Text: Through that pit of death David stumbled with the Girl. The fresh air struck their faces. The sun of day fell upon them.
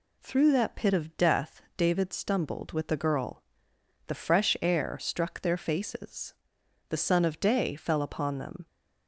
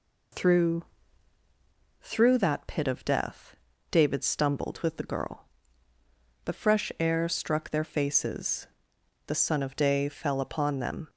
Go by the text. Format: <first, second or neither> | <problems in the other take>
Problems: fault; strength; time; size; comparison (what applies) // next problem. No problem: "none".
first | says "Through" twice; at 2.0 s // pauses between "death" and "David"; slight; at 3.5 s; 0.36 s long